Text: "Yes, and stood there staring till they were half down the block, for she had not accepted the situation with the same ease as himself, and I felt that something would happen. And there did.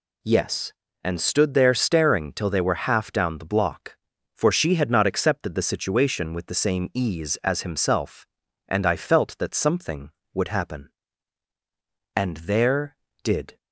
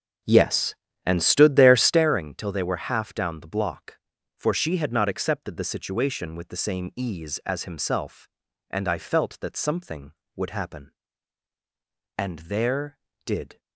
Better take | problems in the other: first | starts louder than the rest; until 2.1 s; 7 dB

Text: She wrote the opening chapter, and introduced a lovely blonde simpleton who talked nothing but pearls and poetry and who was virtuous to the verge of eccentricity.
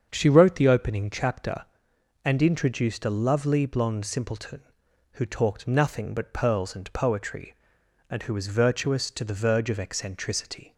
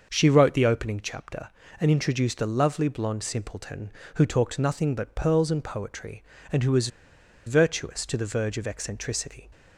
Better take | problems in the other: first | starts louder than the rest; until 1.1 s; 6.5 dB; strong in the first // pauses between "was" and "virtuous"; noticeable; at 6.8 s; 0.57 s long

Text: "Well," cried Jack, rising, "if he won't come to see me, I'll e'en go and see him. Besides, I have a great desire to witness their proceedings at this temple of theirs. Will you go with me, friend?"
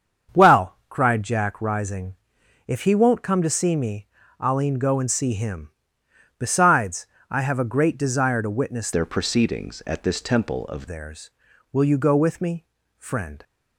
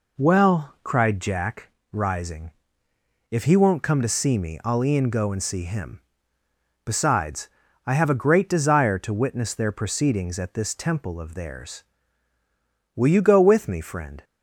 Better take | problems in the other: second | starts louder than the rest; strong; until 1.4 s; 7.5 dB // changes voice from "their" to "of"; from 8.9 to 10.8 s; 1.9 s long

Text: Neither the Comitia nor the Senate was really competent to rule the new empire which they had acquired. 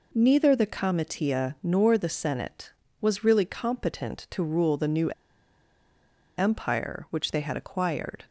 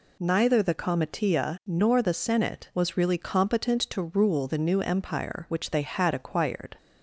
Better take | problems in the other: second | pauses between "new" and "empire"; strong; at 5.1 s; 1.2 s long

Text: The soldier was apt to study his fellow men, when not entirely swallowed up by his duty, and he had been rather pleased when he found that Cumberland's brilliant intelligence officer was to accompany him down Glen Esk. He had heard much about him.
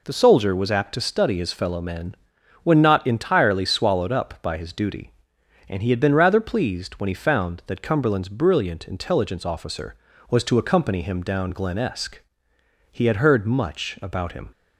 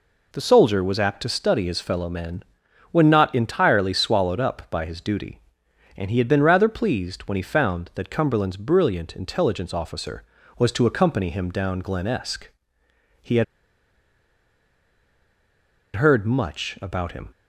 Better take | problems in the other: first | pauses between "had" and "heard"; strong; at 13.4 s; 2.5 s long

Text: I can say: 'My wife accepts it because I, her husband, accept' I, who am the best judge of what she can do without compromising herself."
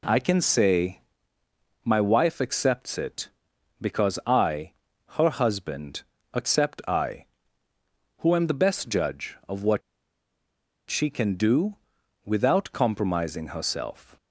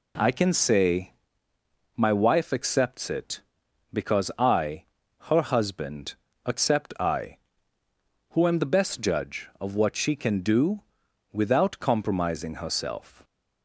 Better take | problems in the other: second | pauses between "what" and "she"; at 9.8 s; 1.0 s long // pauses between "do" and "without"; noticeable; at 11.7 s; 0.50 s long; noticeable in the second

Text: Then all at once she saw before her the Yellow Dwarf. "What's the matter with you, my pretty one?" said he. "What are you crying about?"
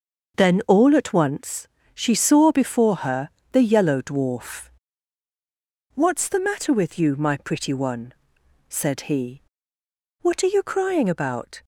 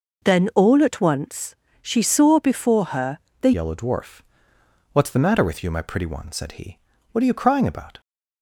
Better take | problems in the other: first | pauses between "once" and "she"; slight; at 1.5 s; 0.26 s long; slight in the first // pauses between "her" and "the"; slight; at 3.1 s; 0.22 s long; slight in the first // changes voice at "Yellow"; from 3.5 s on; 4.5 s long

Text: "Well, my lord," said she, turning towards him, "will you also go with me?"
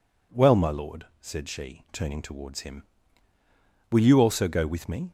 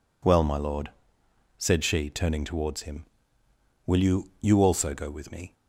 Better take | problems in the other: first | says "you" twice; at 4.3 s

